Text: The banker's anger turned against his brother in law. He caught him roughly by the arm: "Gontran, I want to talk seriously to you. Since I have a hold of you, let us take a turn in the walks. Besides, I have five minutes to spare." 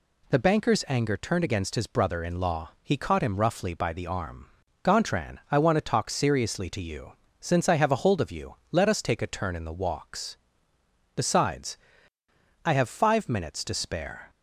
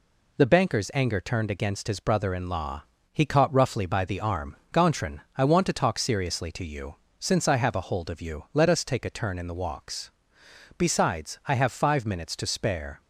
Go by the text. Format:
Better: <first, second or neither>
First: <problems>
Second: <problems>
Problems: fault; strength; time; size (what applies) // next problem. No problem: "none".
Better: first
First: none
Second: skips "him"; at 3.5 s